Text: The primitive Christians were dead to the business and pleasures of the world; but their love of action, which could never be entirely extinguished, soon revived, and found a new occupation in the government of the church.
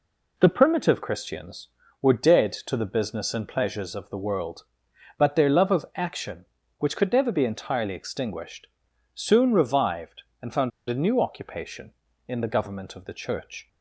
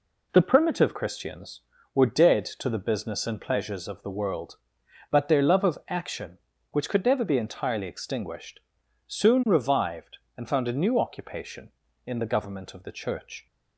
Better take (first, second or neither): second